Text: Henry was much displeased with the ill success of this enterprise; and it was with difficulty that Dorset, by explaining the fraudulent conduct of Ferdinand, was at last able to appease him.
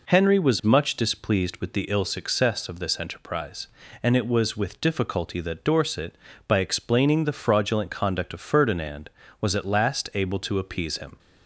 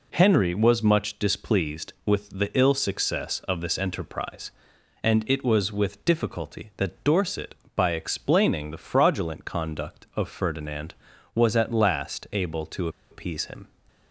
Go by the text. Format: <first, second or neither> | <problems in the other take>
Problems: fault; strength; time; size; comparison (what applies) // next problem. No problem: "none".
first | pauses between "to" and "appease"; slight; at 12.8 s; 0.21 s long